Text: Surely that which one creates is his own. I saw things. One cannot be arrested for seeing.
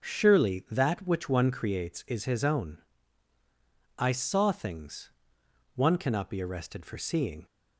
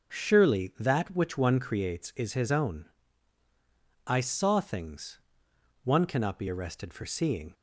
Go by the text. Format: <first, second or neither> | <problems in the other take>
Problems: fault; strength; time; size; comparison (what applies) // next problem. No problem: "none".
neither | none